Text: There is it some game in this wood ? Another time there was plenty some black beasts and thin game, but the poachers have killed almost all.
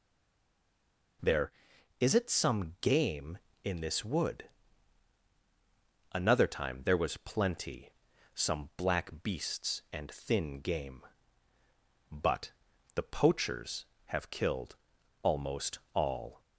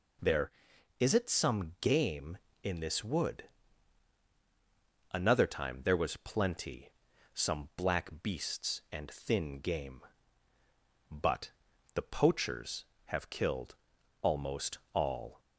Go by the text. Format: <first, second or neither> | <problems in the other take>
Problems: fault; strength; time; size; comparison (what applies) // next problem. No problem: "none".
second | stays silent before the first word; noticeable; until 1.2 s; 1.2 s long // pauses between "plenty" and "some"; at 7.9 s; 0.42 s long; also in the second // pauses between "but" and "the"; at 12.5 s; 0.42 s long; also in the second // pauses between "killed" and "almost"; noticeable; at 14.7 s; 0.46 s long; noticeable in the second // pauses between "almost" and "all"; slight; at 15.7 s; 0.16 s long; slight in the second